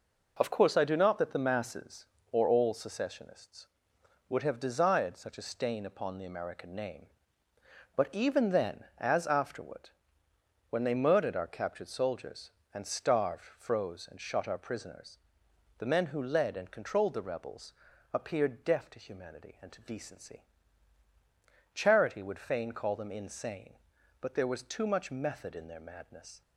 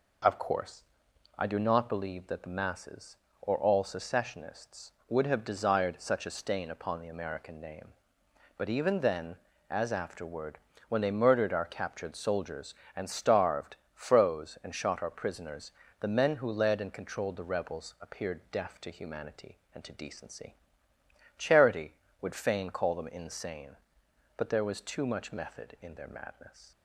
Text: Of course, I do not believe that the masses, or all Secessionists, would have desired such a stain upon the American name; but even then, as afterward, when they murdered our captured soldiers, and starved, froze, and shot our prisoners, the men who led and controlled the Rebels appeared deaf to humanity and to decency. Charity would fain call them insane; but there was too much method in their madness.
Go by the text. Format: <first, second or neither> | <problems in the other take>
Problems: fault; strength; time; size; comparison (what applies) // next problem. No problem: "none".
second | skips "believe"; at 1.1 s // pauses between "Rebels" and "appeared"; at 17.7 s; 0.40 s long